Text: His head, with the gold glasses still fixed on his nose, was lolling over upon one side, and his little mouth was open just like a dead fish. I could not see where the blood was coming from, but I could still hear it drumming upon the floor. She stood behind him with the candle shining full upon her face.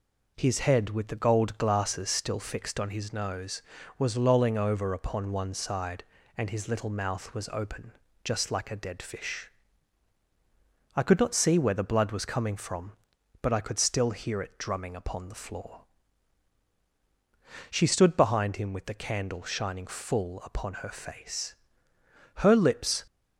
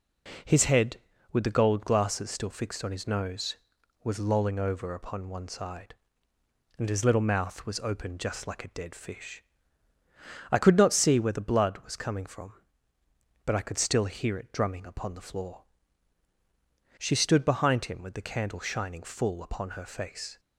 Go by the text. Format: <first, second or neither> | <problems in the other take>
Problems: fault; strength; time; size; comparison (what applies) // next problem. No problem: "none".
second | pauses between "open" and "just"; slight; at 7.9 s; 0.32 s long // goes on to say "Her lips"; noticeable; from 22.3 s on; 0.66 s long